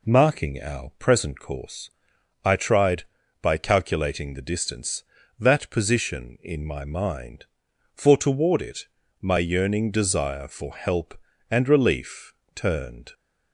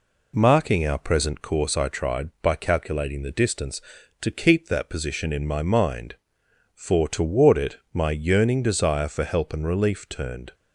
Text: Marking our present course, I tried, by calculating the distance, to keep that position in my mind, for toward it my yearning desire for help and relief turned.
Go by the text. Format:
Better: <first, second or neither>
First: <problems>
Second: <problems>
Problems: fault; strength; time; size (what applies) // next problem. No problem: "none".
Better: second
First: skips "to keep"; at 5.2 s // pauses between "it" and "my"; slight; at 8.8 s; 0.32 s long // pauses between "relief" and "turned"; slight; at 12.3 s; 0.22 s long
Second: pauses between "it" and "my"; slight; at 7.7 s; 0.16 s long